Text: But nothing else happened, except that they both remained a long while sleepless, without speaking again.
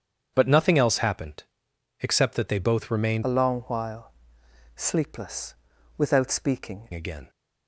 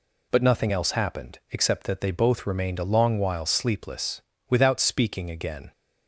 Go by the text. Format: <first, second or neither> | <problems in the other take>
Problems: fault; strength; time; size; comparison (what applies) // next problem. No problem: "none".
second | starts louder than the rest; strong; until 1.3 s; 8 dB // changes voice from "a" to "speaking"; from 3.2 to 6.8 s; 3.6 s long // pauses between "while" and "sleepless"; noticeable; at 4.1 s; 0.64 s long